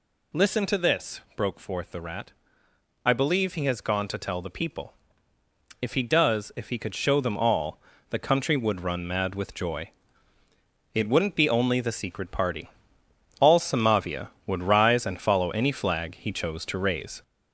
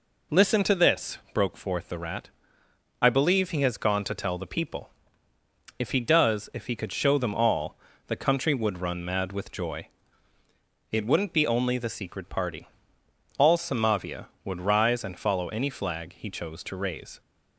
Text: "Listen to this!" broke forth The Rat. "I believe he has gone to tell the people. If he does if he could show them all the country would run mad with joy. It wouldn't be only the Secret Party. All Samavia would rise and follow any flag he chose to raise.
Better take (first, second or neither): second